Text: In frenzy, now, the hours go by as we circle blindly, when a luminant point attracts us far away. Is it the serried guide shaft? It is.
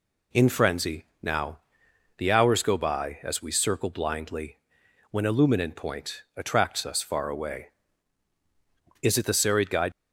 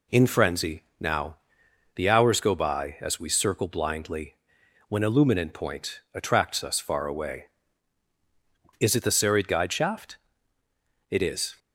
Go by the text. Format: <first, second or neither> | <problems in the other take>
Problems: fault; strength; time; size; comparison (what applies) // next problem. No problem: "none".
second | stops before "shaft It is"; at 9.9 s